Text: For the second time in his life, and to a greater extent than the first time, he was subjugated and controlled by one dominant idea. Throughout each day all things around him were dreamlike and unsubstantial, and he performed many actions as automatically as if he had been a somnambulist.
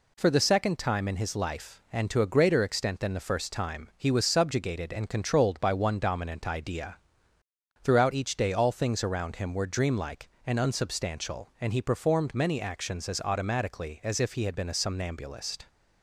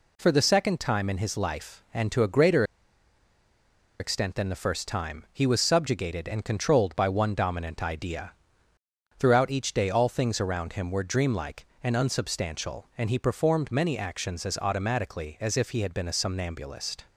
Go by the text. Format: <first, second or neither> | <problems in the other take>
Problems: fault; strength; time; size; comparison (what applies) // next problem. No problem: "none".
first | pauses between "greater" and "extent"; strong; at 2.6 s; 1.3 s long